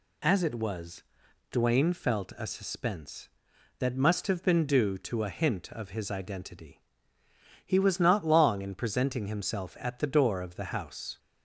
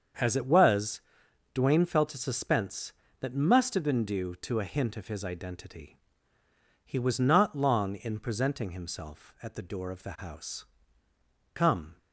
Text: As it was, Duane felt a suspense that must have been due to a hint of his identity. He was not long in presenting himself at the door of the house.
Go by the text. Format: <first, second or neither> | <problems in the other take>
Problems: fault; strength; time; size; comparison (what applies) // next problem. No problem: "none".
first | starts louder than the rest; until 1.7 s; 7 dB // goes on to say "Come"; slight; from 11.5 s on; 0.44 s long